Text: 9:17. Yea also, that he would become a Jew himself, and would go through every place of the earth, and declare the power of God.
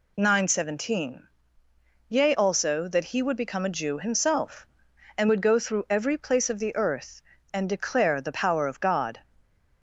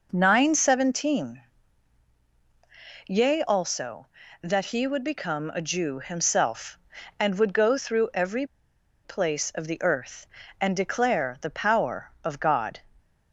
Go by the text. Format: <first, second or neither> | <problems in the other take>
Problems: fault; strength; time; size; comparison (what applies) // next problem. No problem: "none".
first | pauses between "every" and "place"; noticeable; at 8.4 s; 0.57 s long